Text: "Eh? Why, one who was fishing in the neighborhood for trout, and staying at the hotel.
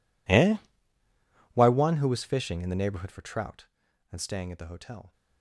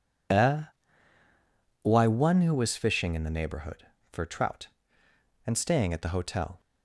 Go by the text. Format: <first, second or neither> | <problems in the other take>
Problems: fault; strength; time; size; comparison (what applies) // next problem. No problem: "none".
second | gets quieter; strong; throughout; 29 dB